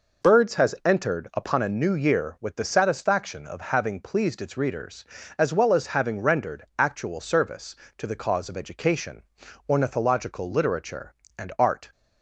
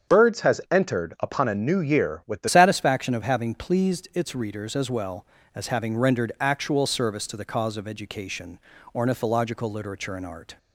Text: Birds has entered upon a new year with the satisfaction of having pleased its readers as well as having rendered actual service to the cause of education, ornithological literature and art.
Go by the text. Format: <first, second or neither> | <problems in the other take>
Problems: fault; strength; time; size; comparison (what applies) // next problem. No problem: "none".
first | starts louder than the rest; strong; until 1.2 s; 7.5 dB // changes voice at "satisfaction"; from 2.4 s on; 8.1 s long